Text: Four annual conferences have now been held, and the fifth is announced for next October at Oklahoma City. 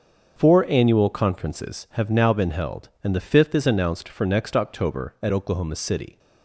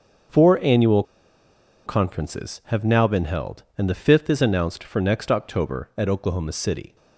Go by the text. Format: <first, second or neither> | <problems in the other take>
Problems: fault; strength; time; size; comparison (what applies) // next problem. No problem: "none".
first | starts louder than the rest; until 2.1 s; 6.5 dB; also in the first // pauses between "annual" and "conferences"; noticeable; at 1.0 s; 0.83 s long